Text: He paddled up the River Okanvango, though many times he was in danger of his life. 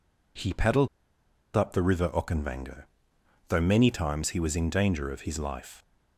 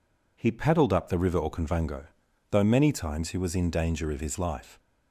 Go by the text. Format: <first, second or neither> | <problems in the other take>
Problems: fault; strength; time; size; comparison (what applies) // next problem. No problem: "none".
second | pauses between "paddled" and "up"; noticeable; at 0.8 s; 0.68 s long